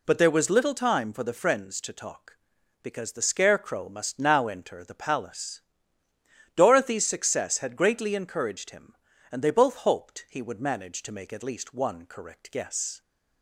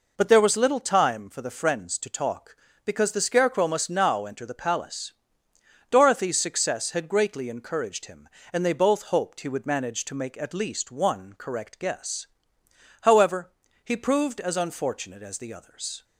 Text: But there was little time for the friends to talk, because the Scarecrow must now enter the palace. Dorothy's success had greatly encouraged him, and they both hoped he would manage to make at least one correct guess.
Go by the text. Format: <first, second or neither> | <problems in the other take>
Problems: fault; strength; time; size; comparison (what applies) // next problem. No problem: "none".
first | goes on to say "However he proved as unfortunate as the others"; strong; from 13.0 s on; 3.0 s long